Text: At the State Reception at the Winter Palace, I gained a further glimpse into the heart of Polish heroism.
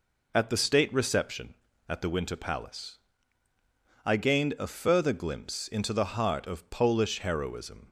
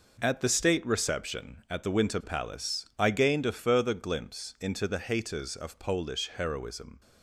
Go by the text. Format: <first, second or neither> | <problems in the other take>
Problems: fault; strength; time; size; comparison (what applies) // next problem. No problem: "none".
first | says "haters" for "heart"; at 4.9 s